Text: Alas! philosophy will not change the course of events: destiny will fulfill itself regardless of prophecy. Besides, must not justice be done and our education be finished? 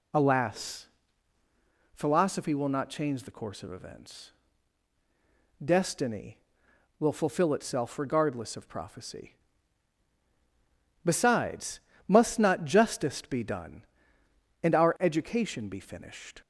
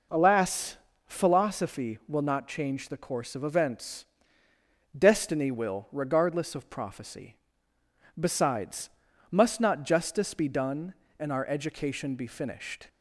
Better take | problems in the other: first | skips "fulfill itself"; at 5.8 s

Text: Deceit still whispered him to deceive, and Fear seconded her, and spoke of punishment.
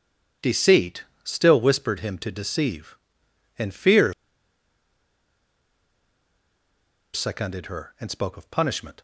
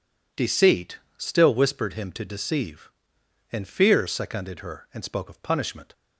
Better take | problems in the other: second | pauses between "Deceit" and "still"; slight; at 1.0 s; 0.22 s long; slight in the second // pauses between "Fear" and "seconded"; strong; at 4.1 s; 3.0 s long

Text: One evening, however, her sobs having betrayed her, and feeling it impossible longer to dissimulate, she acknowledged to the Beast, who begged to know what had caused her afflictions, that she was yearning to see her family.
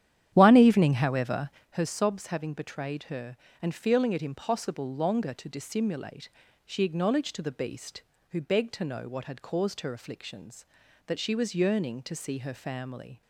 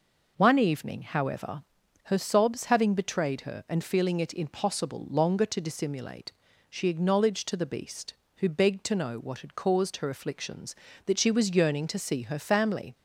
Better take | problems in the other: second | starts louder than the rest; strong; until 1.8 s; 10.5 dB

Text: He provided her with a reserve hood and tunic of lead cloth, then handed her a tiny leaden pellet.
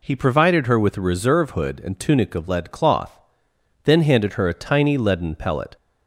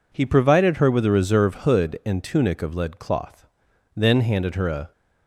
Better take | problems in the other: first | stops before "tiny leaden pellet"; at 4.9 s

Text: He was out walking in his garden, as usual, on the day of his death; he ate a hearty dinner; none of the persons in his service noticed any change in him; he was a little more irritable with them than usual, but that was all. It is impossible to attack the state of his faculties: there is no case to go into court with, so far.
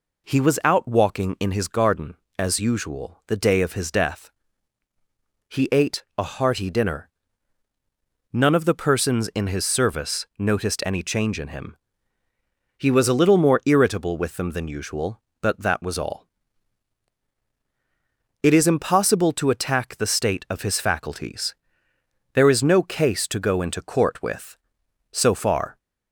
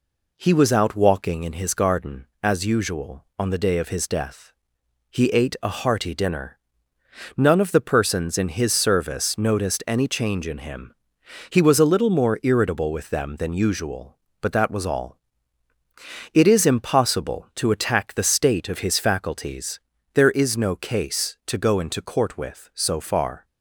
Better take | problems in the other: second | skips "on"; at 3.2 s

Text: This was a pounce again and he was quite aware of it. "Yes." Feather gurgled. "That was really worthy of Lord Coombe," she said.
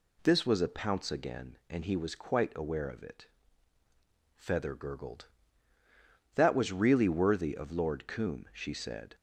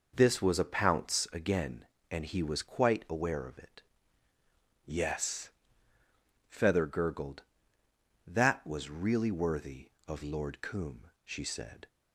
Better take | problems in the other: second | skips "Yes"; at 3.8 s

